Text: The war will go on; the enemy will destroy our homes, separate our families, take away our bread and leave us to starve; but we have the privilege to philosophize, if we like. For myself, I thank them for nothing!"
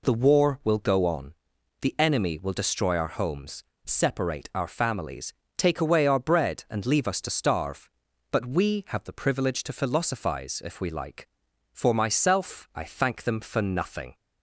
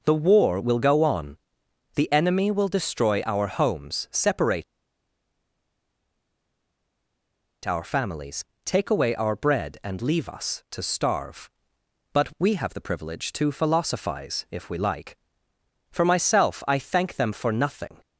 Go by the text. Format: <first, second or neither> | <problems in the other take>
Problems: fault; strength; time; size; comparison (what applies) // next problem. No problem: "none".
first | pauses between "separate" and "our"; strong; at 4.6 s; 3.0 s long